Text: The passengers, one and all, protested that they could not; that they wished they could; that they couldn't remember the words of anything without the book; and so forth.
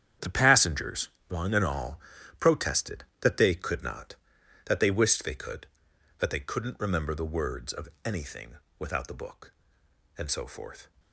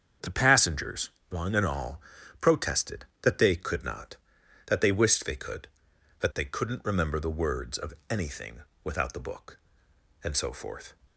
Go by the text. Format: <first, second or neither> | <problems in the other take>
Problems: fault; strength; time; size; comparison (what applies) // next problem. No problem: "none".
second | gets quieter; strong; throughout; 12 dB // starts louder than the rest; strong; until 1.4 s; 9 dB; strong in the second // pauses between "of" and "anything"; slight; at 7.8 s; 0.16 s long; slight in the second // pauses between "anything" and "without"; slight; at 8.5 s; 0.22 s long; slight in the second